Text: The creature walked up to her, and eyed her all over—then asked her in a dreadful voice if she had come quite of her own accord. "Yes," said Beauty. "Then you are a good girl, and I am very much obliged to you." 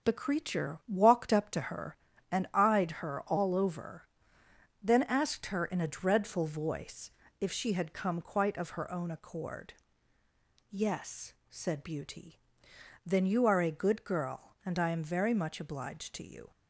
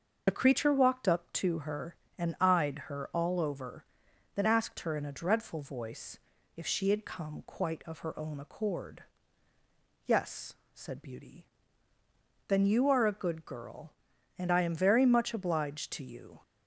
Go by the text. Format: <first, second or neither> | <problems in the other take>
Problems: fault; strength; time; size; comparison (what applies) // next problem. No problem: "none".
first | loses the start of "The"; at 0.2 s; 35 ms // starts louder than the rest; until 1.2 s; 6 dB; strong in the first // pauses between "voice" and "if"; at 6.1 s; 0.38 s long; slight in the first